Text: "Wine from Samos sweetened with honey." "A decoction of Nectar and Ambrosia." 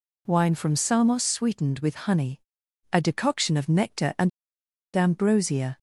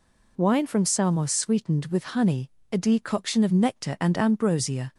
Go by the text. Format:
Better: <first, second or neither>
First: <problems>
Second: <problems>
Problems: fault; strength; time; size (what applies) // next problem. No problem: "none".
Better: second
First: pauses between "and" and "Ambrosia"; noticeable; at 4.2 s; 0.66 s long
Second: none